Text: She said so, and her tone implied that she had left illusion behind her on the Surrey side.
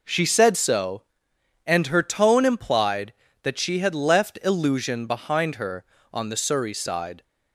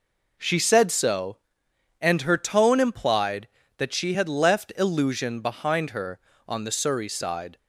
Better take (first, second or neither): neither